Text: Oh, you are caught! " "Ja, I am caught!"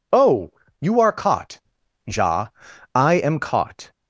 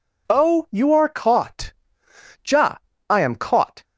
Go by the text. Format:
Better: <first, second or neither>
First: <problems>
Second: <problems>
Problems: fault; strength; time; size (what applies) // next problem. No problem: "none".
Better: neither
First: none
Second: none